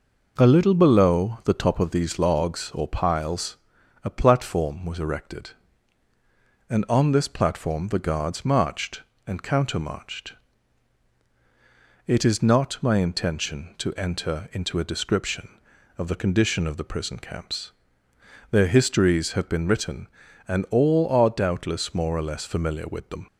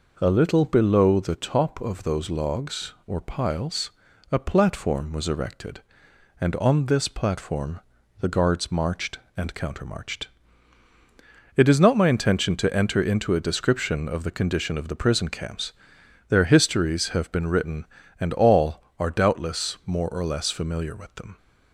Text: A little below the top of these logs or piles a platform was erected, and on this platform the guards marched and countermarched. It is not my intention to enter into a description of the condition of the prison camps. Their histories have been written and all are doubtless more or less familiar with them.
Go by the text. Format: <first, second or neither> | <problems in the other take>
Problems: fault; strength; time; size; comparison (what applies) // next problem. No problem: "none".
first | says "those" for "these"; at 2.0 s // pauses between "piles" and "a"; at 3.9 s; 0.40 s long; noticeable in the first // pauses between "platform" and "the"; at 7.8 s; 0.40 s long